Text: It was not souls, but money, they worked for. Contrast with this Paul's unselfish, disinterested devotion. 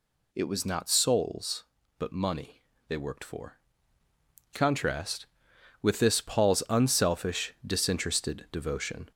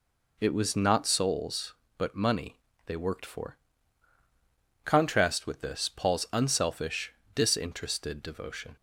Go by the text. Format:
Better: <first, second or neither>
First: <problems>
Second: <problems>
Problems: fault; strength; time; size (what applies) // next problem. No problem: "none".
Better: second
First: gets louder; throughout; 3.5 dB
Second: none